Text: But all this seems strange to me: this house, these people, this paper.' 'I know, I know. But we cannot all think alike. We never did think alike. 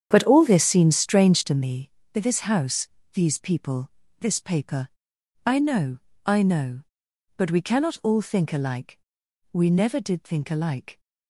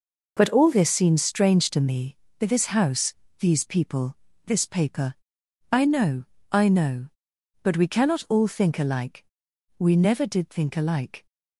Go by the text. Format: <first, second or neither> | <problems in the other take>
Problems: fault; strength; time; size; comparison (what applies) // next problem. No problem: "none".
second | starts louder than the rest; strong; until 1.6 s; 8.5 dB